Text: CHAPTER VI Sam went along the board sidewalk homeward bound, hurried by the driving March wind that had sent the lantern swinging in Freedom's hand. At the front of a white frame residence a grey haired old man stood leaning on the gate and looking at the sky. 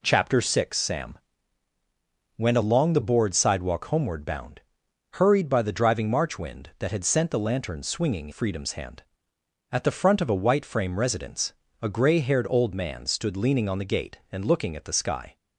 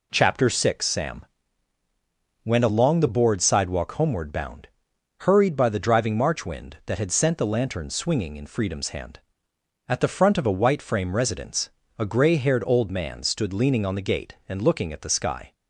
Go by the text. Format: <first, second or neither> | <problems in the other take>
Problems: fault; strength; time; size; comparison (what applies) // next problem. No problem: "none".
second | pauses between "Sam" and "went"; at 1.1 s; 1.2 s long; also in the second // skips "in"; at 8.2 s // pauses between "residence" and "a"; slight; at 11.5 s; 0.28 s long; slight in the second